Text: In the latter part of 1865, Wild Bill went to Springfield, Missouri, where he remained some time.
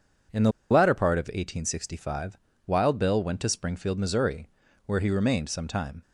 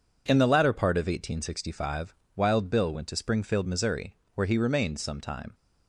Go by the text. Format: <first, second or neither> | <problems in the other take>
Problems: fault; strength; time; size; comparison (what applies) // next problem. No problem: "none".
second | pauses between "the" and "latter"; slight; at 0.5 s; 0.20 s long